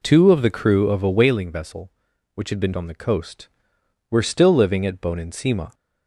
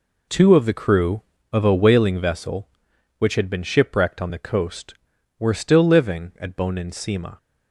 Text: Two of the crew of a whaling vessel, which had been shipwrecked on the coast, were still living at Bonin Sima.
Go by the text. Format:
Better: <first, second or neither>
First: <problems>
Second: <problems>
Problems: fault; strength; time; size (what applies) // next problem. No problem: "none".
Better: second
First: skips "shipwrecked"; at 2.7 s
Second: none